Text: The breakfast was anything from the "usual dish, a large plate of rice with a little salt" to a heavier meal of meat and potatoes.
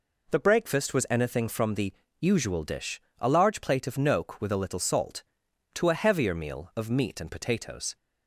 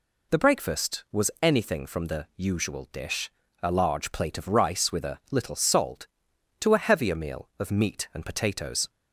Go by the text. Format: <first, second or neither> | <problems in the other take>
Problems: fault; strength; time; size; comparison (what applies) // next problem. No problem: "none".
second | pauses between "the" and "usual"; slight; at 1.9 s; 0.26 s long // says "noke" for "rice"; at 3.9 s